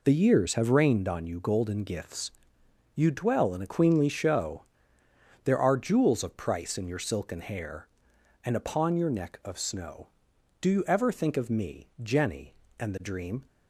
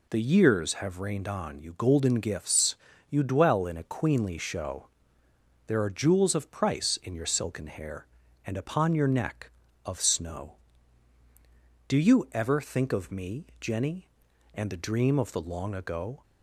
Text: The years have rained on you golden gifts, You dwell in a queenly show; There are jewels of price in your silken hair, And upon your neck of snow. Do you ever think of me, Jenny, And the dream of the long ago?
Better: second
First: stops before "of the long ago"; at 13.4 s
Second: none

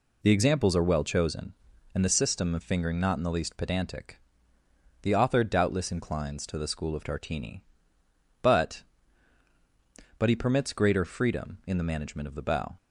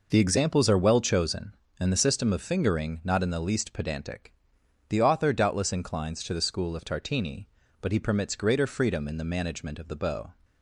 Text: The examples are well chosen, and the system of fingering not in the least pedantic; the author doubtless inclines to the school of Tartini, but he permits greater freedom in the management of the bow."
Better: second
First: says "but" twice; at 10.1 s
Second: none

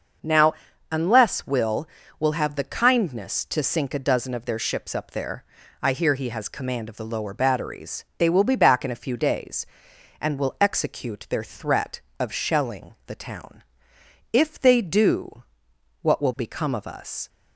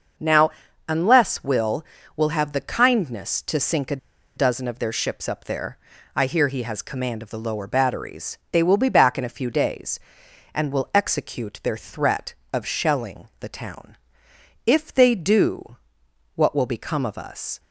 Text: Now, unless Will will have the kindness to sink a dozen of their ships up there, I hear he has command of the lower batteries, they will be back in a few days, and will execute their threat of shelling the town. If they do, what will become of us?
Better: first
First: starts louder than the rest; noticeable; until 1.6 s; 6 dB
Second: starts louder than the rest; noticeable; until 1.5 s; 6 dB // pauses between "a" and "dozen"; at 3.9 s; 0.39 s long

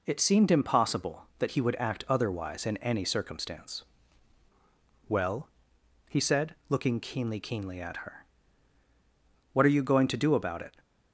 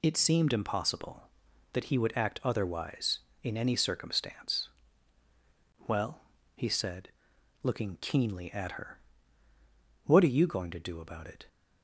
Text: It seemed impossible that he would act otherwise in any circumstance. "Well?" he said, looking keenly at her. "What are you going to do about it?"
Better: second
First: says "keenly" twice; at 7.4 s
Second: none

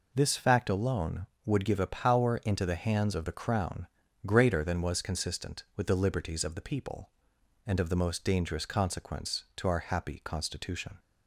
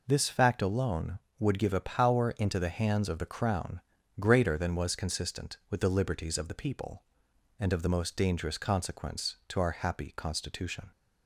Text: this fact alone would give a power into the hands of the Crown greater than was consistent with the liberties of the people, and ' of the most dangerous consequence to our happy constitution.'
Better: neither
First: pauses between "Crown" and "greater"; at 3.8 s; 0.38 s long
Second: pauses between "Crown" and "greater"; at 3.8 s; 0.38 s long

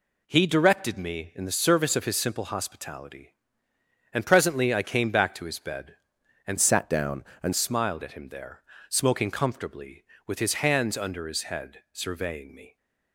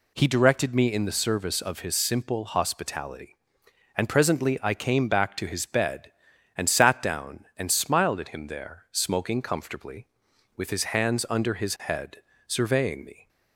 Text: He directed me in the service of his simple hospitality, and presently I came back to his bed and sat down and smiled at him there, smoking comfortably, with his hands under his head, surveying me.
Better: second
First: changes voice from "sat" to "and"; from 6.5 to 7.5 s; 1.0 s long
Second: none

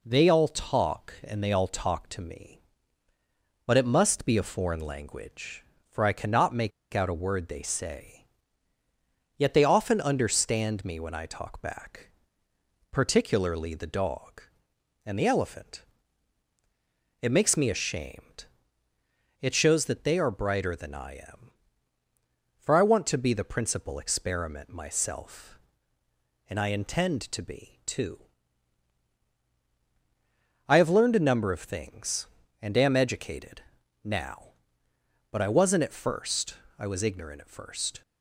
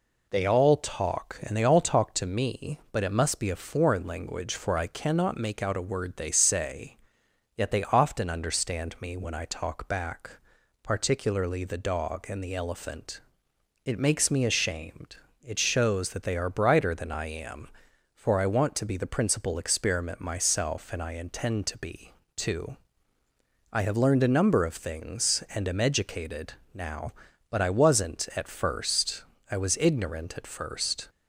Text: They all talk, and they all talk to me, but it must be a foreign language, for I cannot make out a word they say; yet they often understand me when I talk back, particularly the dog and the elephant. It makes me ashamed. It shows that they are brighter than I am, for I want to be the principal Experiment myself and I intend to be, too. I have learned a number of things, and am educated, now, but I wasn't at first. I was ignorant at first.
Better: second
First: pauses between "make" and "out"; slight; at 6.7 s; 0.22 s long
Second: none

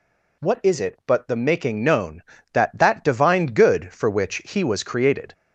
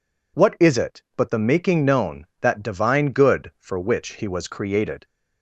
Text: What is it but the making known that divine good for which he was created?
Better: second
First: says "that" twice; at 2.7 s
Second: none

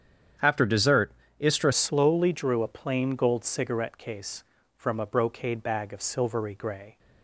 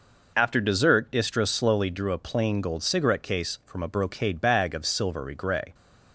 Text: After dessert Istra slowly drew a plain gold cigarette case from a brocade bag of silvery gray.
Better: second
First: starts louder than the rest; strong; until 1.6 s; 8.5 dB // pauses between "dessert" and "Istra"; slight; at 1.1 s; 0.28 s long // changes voice at "slowly"; from 1.7 s on; 5.2 s long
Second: none

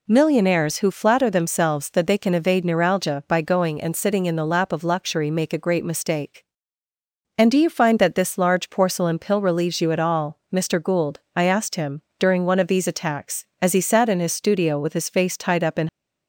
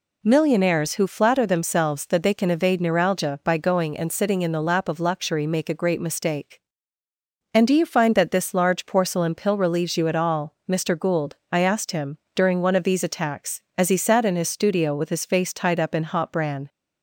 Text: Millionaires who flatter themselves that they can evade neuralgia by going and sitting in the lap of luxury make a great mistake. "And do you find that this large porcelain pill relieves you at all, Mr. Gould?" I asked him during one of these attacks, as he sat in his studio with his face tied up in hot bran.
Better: second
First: pauses between "him" and "during"; slight; at 12.0 s; 0.16 s long // stops before "hot bran"; at 15.8 s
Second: pauses between "him" and "during"; slight; at 12.1 s; 0.16 s long

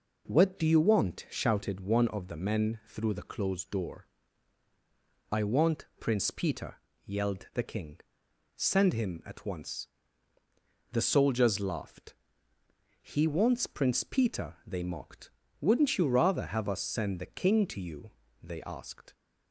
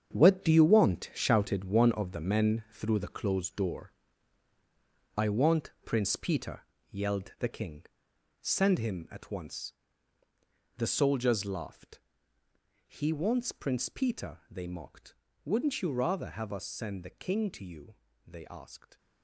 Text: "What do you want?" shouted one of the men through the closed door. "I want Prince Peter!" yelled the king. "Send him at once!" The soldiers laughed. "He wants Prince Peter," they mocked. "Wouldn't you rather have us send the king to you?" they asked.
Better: first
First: none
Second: gets quieter; strong; throughout; 10 dB

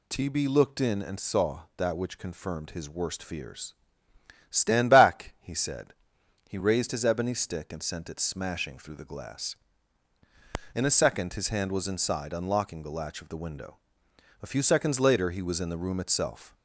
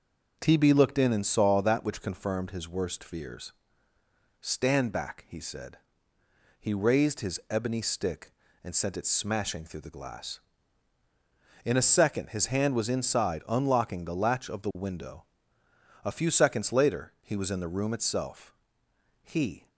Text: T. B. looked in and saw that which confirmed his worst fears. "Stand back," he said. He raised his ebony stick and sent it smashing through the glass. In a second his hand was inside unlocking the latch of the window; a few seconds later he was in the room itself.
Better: first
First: none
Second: goes on to say "He"; slight; from 19.2 s on; 0.46 s long

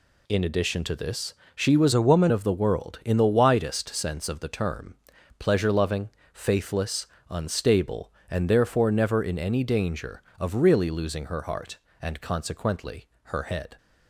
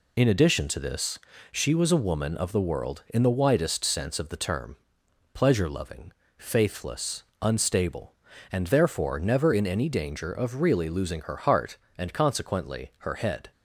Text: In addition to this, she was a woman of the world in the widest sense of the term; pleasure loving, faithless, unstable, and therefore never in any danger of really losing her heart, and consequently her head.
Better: second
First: changes voice from "a" to "woman"; from 1.9 to 2.3 s; 0.4 s long // pauses between "consequently" and "her"; slight; at 13.0 s; 0.20 s long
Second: none

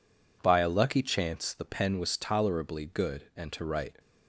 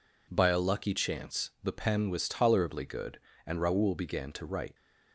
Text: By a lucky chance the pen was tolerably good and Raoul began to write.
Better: second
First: skips "Raoul began"; at 3.5 s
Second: none

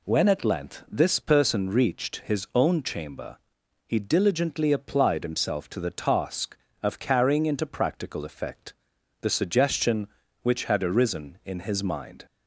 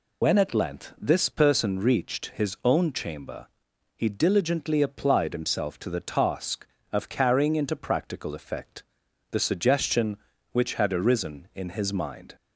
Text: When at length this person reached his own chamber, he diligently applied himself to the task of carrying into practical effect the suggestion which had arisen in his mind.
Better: first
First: pauses between "effect" and "the"; noticeable; at 8.7 s; 0.48 s long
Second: loses the start of "When"; at 0.2 s; 75 ms // pauses between "effect" and "the"; noticeable; at 8.8 s; 0.48 s long

